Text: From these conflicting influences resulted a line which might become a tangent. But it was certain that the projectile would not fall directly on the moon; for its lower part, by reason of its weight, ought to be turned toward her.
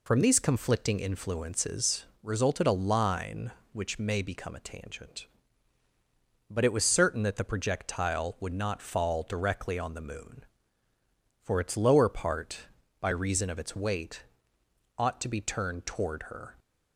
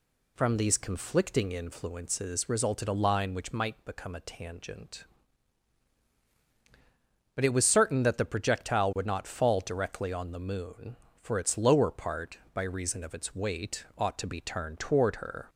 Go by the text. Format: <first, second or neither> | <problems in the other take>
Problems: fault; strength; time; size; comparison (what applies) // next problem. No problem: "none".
second | pauses between "influences" and "resulted"; slight; at 2.0 s; 0.18 s long // says "may" for "might"; at 3.9 s